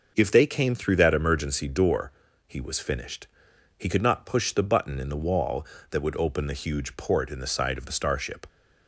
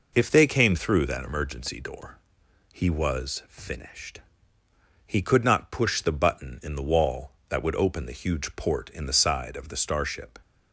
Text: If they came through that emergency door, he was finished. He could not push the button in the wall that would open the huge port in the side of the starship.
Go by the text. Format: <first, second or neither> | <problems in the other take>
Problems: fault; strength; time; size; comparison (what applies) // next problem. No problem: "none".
neither | none